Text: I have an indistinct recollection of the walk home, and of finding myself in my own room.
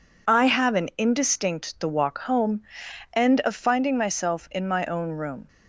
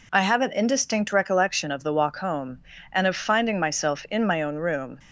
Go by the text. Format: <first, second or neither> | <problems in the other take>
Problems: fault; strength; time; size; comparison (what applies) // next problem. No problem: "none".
second | skips "recollection of"; at 1.7 s